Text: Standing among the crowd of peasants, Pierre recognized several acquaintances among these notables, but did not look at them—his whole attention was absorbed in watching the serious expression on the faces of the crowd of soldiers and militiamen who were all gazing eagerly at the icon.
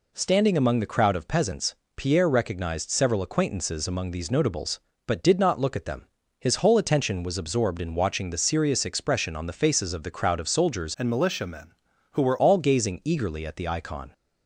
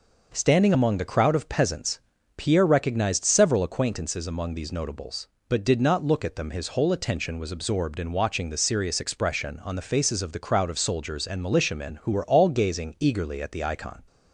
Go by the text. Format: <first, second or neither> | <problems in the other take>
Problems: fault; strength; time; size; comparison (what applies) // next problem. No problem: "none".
second | changes voice from "and" to "were"; from 10.9 to 12.3 s; 1.4 s long